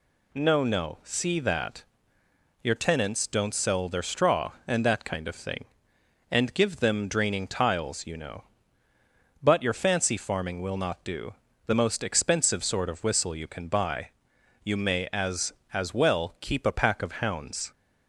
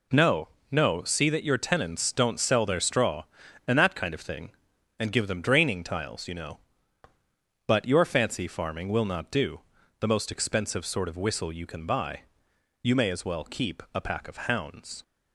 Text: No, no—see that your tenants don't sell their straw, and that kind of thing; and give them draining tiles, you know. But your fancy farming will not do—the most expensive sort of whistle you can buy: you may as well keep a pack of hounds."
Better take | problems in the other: second | pauses between "that" and "your"; noticeable; at 1.8 s; 0.78 s long // says "as" twice; at 15.7 s

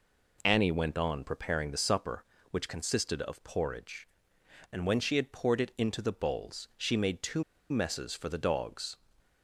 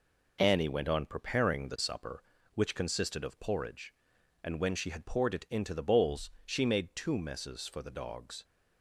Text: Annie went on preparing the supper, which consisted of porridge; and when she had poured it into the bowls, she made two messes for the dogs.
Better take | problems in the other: second | pauses between "two" and "messes"; slight; at 7.4 s; 0.26 s long

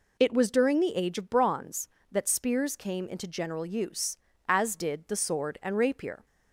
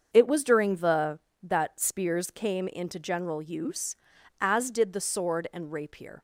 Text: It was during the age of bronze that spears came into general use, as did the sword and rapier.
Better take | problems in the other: first | starts louder than the rest; until 1.1 s; 7 dB // skips "age of bronze"; at 1.3 s

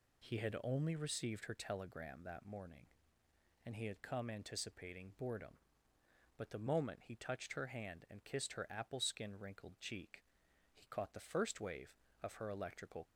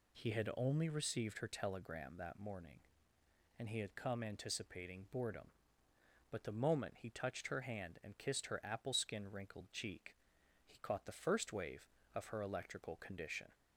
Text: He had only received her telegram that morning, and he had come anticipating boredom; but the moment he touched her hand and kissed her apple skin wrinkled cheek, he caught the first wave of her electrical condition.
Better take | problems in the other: second | stops before "condition"; at 13.0 s

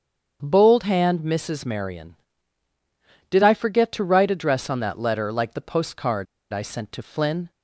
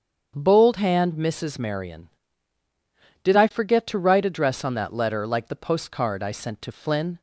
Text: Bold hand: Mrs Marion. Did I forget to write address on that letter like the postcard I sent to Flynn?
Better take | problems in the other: second | starts louder than the rest; strong; until 1.4 s; 7.5 dB; strong in the second // pauses between "postcard" and "I"; slight; at 6.2 s; 0.26 s long

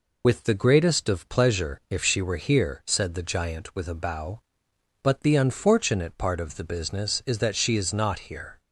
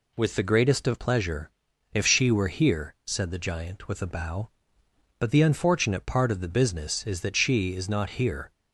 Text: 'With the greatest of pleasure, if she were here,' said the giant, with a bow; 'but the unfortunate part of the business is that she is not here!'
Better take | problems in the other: second | loses the start of "With"; at 0.2 s; 50 ms

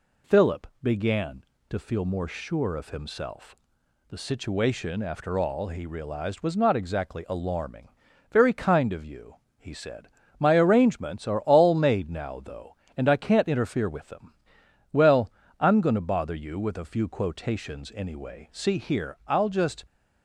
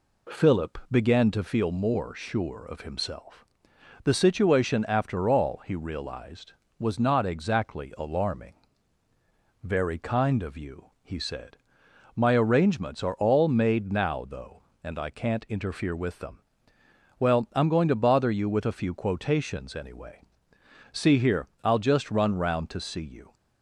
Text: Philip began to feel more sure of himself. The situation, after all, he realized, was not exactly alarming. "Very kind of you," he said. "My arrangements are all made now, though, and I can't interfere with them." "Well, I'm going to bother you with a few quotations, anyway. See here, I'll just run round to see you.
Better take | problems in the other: second | pauses between "Philip" and "began"; slight; at 0.6 s; 0.16 s long // stops before "run round to see you"; at 19.8 s

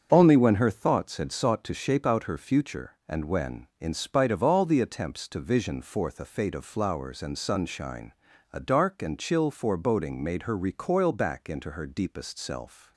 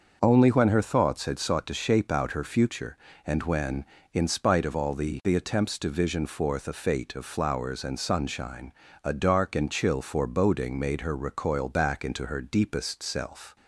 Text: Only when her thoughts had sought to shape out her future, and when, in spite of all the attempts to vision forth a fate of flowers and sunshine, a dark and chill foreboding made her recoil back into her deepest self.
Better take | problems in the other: first | starts louder than the rest; until 1.2 s; 6.5 dB; strong in the first // says "the" twice; at 5.2 s

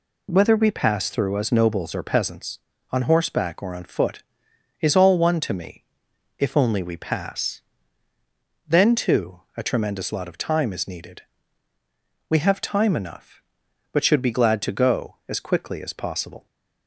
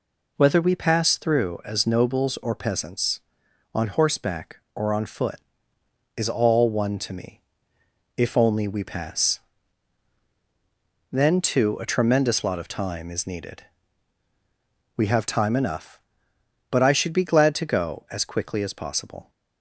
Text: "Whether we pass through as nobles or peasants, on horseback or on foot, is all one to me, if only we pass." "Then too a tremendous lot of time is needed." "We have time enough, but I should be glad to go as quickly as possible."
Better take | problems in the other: second | skips "I"; at 14.0 s

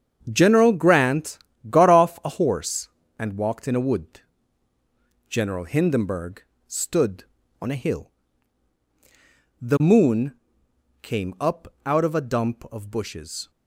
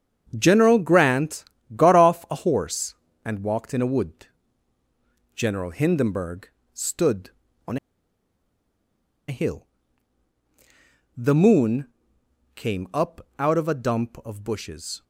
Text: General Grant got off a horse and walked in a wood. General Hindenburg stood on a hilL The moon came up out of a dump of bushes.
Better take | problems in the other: first | starts louder than the rest; strong; until 1.3 s; 7.5 dB; strong in the first // pauses between "Grant" and "got"; slight; at 1.4 s; 0.28 s long; slight in the first // pauses between "Hindenburg" and "stood"; slight; at 6.4 s; 0.24 s long; slight in the first // pauses between "on" and "a"; strong; at 7.7 s; 1.5 s long // pauses between "hilL" and "The"; strong; at 9.6 s; 1.4 s long; strong in the first // pauses between "moon" and "came"; noticeable; at 11.8 s; 0.68 s long; noticeable in the first

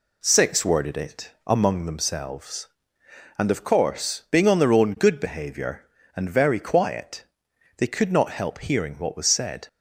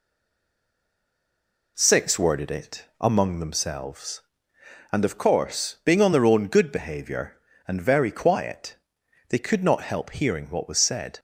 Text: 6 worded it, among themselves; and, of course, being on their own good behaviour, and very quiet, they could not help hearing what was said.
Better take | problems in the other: first | stays silent before the first word; noticeable; until 1.7 s; 1.7 s long

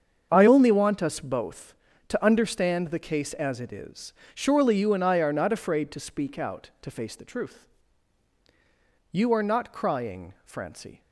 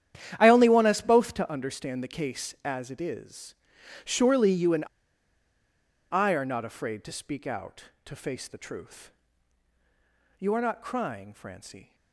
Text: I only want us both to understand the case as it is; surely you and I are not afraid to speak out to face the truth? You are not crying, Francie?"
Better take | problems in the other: first | starts louder than the rest; strong; until 1.3 s; 10.5 dB; strong in the first // pauses between "and" and "I"; strong; at 4.8 s; 1.2 s long

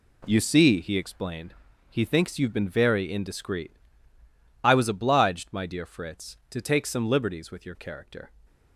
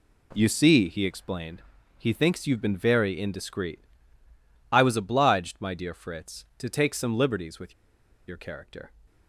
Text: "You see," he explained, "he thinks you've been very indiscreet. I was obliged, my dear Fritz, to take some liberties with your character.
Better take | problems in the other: first | pauses between "with" and "your"; noticeable; at 7.7 s; 0.54 s long

